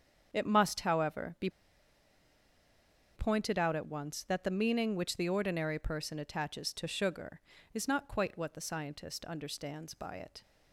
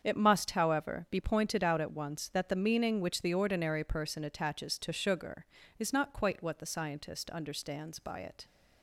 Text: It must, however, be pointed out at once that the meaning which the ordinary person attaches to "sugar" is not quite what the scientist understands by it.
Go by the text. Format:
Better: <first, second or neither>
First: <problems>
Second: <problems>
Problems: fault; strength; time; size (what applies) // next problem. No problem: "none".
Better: second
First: starts louder than the rest; strong; until 1.3 s; 7.5 dB // pauses between "be" and "pointed"; strong; at 1.4 s; 1.6 s long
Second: starts louder than the rest; strong; until 1.0 s; 7.5 dB